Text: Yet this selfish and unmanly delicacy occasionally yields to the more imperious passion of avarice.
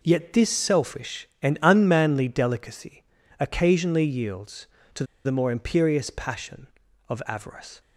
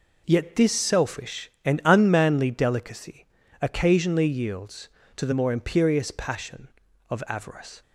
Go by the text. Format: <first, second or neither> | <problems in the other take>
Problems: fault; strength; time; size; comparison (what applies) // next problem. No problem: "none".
second | pauses between "delicacy" and "occasionally"; slight; at 3.0 s; 0.36 s long; slight in the second // pauses between "to" and "the"; slight; at 5.0 s; 0.21 s long